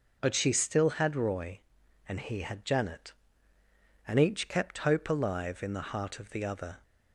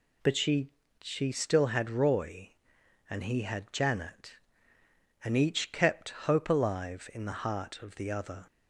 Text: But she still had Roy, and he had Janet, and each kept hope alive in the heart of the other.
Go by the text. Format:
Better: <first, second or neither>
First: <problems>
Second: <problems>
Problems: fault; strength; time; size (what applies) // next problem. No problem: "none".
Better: first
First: none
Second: says "she" twice; at 1.0 s